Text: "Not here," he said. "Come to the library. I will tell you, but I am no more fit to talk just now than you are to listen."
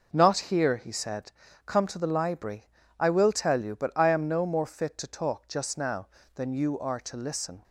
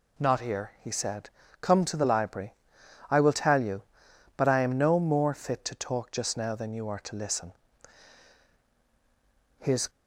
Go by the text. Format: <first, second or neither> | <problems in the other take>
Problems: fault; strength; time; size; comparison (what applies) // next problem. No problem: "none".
first | goes on to say "His"; slight; from 9.5 s on; 0.32 s long